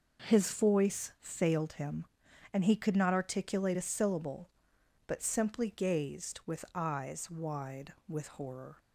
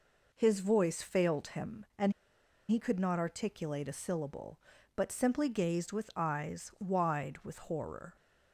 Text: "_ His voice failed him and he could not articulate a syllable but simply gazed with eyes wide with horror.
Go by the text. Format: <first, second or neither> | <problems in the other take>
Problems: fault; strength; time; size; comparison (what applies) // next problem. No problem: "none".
first | pauses between "and" and "he"; noticeable; at 2.1 s; 0.57 s long